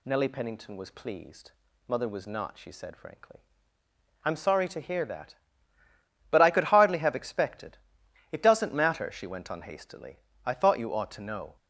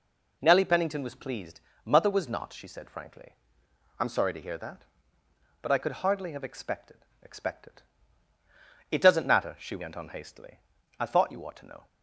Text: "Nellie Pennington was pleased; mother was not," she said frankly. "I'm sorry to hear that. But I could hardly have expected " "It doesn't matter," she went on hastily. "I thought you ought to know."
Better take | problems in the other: first | says "expected" twice; at 7.2 s

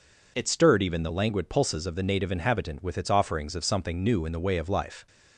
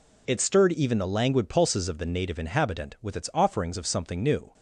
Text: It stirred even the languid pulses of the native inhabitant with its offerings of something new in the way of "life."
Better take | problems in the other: first | stops before "in the way of life"; at 4.5 s

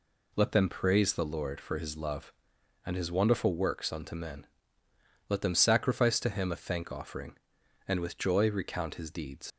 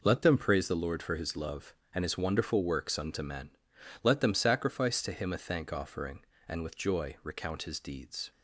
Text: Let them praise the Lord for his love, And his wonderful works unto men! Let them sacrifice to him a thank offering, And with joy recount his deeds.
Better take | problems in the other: second | leaves "deeds" unfinished; at 9.5 s; 80 ms

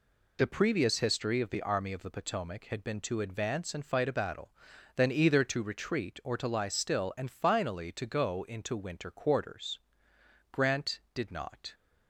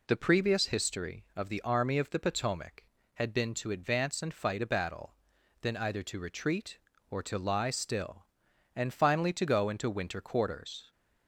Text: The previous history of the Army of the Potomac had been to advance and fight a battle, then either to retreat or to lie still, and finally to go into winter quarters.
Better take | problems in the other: second | goes on to say "Grant did not"; noticeable; from 10.4 s on; 1.2 s long

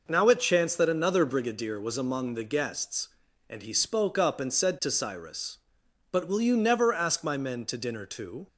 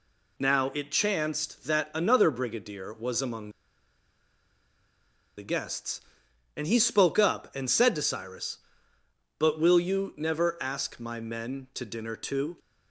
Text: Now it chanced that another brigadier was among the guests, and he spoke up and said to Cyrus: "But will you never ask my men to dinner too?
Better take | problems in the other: first | pauses between "among" and "the"; strong; at 3.5 s; 1.8 s long

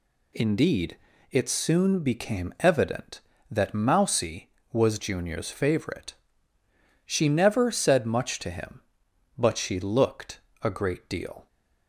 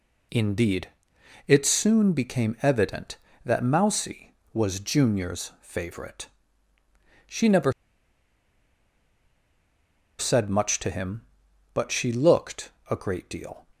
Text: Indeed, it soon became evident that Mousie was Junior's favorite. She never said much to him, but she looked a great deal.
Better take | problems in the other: first | pauses between "never" and "said"; strong; at 7.7 s; 2.4 s long // pauses between "looked" and "a"; slight; at 12.7 s; 0.18 s long; slight in the first

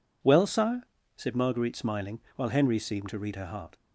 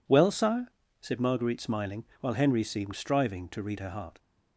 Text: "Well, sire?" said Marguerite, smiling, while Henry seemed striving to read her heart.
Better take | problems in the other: second | skips "striving"; at 3.0 s

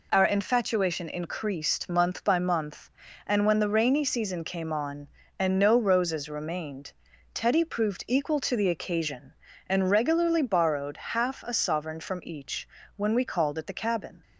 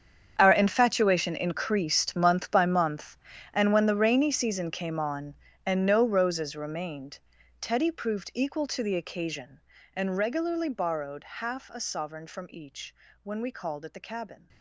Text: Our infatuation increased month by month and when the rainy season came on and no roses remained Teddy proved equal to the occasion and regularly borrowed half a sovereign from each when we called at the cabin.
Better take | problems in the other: first | gets quieter; strong; throughout; 16.5 dB // pauses between "remained" and "Teddy"; at 7.1 s; 0.42 s long; also in the first // pauses between "each" and "when"; slight; at 12.9 s; 0.28 s long; slight in the first

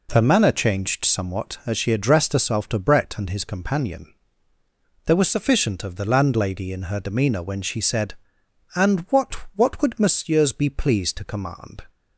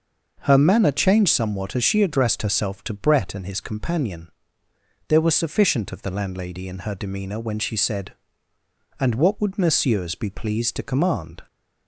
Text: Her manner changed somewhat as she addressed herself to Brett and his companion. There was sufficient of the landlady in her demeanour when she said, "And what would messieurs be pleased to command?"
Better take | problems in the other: second | says "what" twice; at 9.5 s

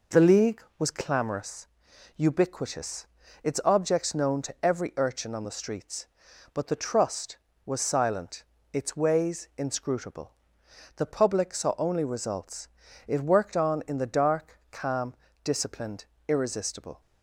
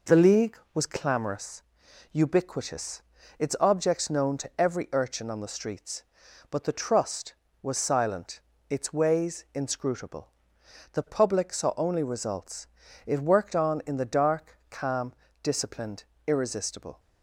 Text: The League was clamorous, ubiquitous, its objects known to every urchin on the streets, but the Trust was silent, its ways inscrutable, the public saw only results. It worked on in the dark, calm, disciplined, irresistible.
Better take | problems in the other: neither | none

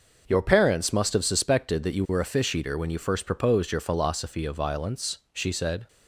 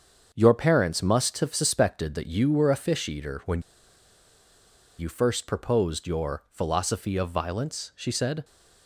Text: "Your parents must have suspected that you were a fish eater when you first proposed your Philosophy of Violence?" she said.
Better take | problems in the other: first | starts louder than the rest; until 1.3 s; 7 dB // pauses between "when" and "you"; strong; at 3.5 s; 1.3 s long

